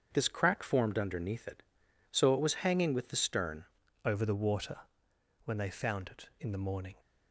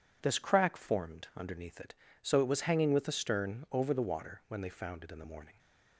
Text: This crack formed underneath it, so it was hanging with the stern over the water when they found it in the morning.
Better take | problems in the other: second | starts louder than the rest; until 1.1 s; 7 dB // changes voice at "over"; from 4.0 s on; 2.9 s long // pauses between "water" and "when"; noticeable; at 4.7 s; 0.66 s long

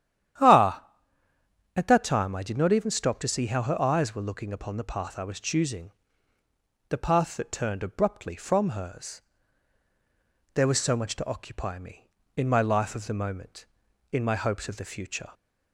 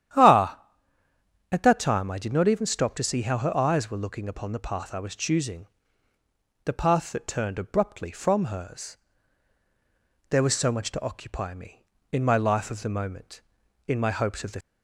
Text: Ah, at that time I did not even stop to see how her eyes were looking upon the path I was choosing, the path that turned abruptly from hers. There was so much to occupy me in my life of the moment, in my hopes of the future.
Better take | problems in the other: first | starts louder than the rest; strong; until 2.0 s; 10.5 dB; strong in the first // stops before "future"; at 14.6 s

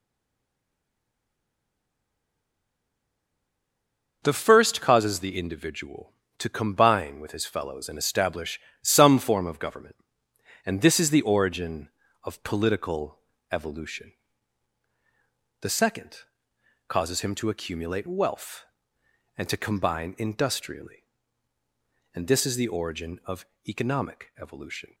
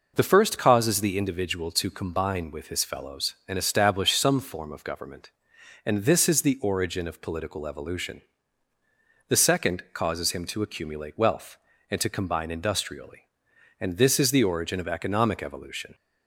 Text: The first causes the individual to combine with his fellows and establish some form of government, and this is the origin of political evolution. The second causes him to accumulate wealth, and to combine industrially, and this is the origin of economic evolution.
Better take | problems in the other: second | stays silent before the first word; strong; until 4.2 s; 4.2 s long // pauses between "establish" and "some"; slight; at 8.6 s; 0.20 s long // pauses between "political" and "evolution"; slight; at 13.1 s; 0.32 s long // pauses between "second" and "causes"; noticeable; at 16.1 s; 0.68 s long // pauses between "of" and "economic"; slight; at 23.4 s; 0.24 s long

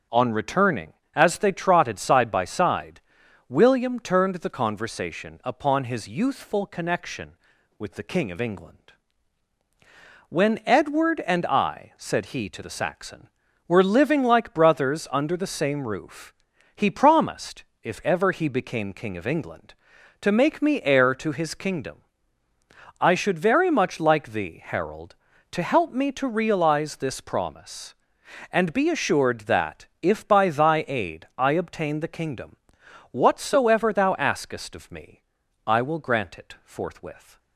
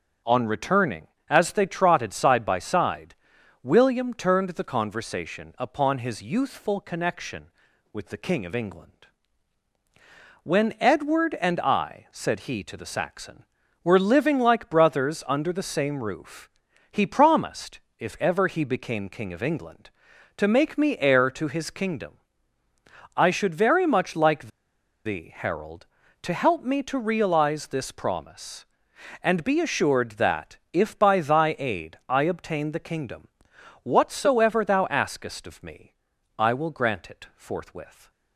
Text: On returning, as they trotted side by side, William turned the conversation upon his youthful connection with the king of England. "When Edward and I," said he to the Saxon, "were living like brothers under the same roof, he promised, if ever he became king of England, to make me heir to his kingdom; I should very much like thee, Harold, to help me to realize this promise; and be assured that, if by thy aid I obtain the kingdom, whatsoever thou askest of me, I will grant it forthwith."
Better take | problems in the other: first | starts louder than the rest; strong; until 1.4 s; 7 dB; also in the first // pauses between "like" and "thee"; noticeable; at 24.4 s; 0.56 s long

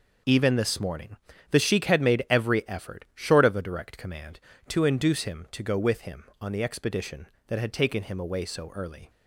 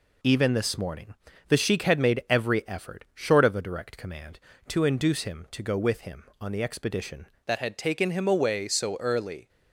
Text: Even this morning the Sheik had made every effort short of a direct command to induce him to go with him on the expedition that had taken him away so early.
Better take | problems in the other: first | pauses between "morning" and "the"; slight; at 1.1 s; 0.32 s long; slight in the first // changes voice at "that"; from 7.4 s on; 2.0 s long

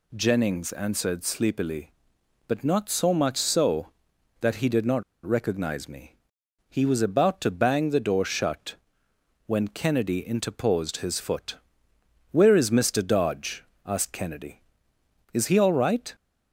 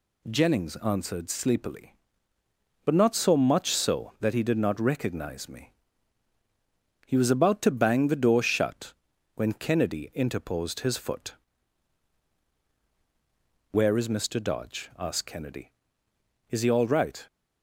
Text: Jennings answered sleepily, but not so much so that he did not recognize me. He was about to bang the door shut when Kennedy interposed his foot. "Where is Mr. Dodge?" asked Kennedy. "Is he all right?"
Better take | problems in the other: second | pauses between "not" and "recognize"; slight; at 5.0 s; 0.21 s long // pauses between "shut" and "when"; noticeable; at 8.7 s; 0.72 s long; also in the second

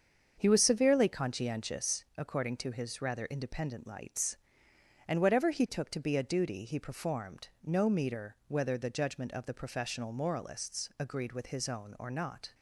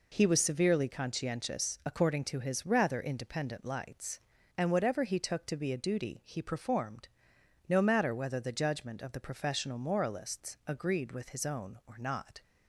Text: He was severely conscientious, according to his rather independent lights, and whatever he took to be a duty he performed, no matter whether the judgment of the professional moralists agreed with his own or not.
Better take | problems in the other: second | starts louder than the rest; until 1.3 s; 7 dB // says "meter" for "matter"; at 7.9 s

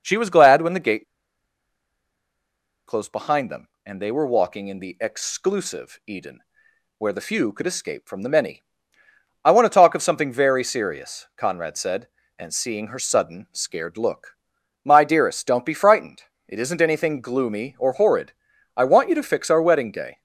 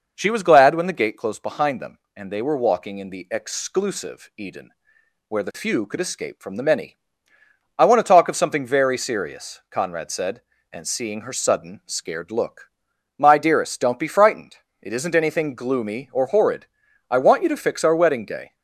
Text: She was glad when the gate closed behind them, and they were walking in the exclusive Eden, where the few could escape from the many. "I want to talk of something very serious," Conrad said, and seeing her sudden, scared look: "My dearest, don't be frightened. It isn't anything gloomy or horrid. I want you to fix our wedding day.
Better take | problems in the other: second | pauses between "gate" and "closed"; strong; at 1.0 s; 1.8 s long

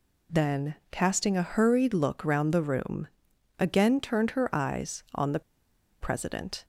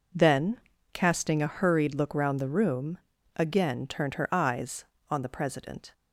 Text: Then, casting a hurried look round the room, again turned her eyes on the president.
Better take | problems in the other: second | pauses between "the" and "president"; noticeable; at 5.4 s; 0.60 s long

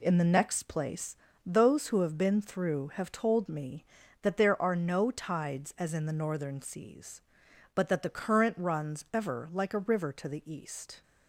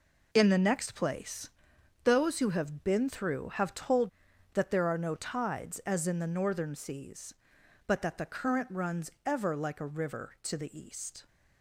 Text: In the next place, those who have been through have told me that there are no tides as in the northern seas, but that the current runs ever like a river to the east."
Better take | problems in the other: first | skips "me"; at 4.3 s // pauses between "runs" and "ever"; slight; at 9.0 s; 0.16 s long

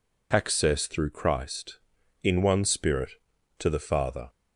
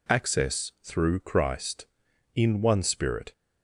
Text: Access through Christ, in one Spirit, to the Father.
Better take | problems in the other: first | stops before "to the Father"; at 3.3 s

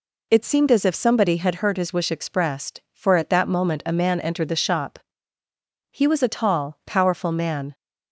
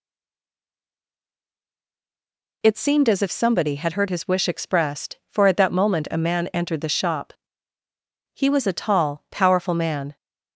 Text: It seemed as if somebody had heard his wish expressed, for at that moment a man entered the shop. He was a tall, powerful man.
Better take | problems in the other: first | stays silent before the first word; strong; until 2.6 s; 2.6 s long

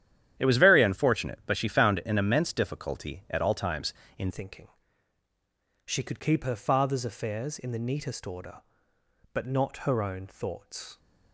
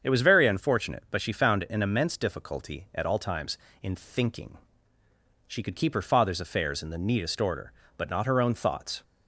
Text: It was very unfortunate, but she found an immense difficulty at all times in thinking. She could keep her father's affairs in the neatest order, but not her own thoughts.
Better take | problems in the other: second | starts louder than the rest; strong; until 1.3 s; 11 dB; strong in the second // changes voice at "thinking"; from 4.3 s on; 6.6 s long

